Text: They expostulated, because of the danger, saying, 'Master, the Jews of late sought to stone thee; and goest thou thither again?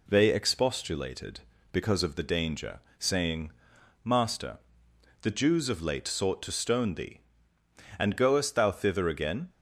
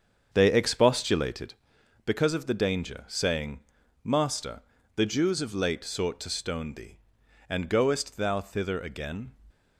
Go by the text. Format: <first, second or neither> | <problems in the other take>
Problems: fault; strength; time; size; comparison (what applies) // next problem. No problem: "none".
first | starts louder than the rest; strong; until 1.6 s; 7 dB